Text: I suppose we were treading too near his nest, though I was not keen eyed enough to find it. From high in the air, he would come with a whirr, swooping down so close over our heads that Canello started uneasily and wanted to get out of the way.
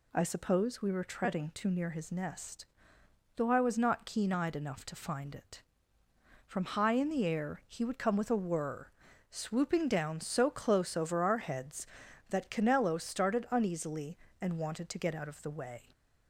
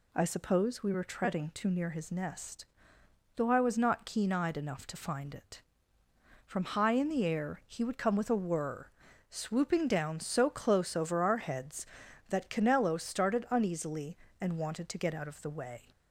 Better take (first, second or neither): neither